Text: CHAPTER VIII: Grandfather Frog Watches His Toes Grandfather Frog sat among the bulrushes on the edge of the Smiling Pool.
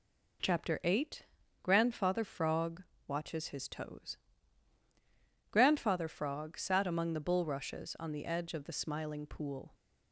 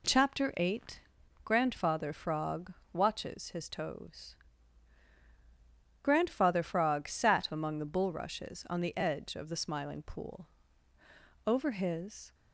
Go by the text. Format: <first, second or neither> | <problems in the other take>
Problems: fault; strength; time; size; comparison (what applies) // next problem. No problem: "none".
first | pauses between "Frog" and "Watches"; slight; at 2.7 s; 0.22 s long; slight in the first // pauses between "Toes" and "Grandfather"; strong; at 4.3 s; 1.6 s long; strong in the first // goes on to say "Over his"; noticeable; from 11.4 s on; 0.88 s long